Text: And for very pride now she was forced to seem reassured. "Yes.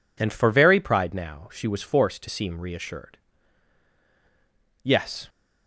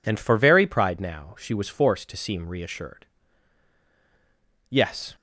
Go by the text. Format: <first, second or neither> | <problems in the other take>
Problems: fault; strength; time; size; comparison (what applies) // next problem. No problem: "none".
neither | none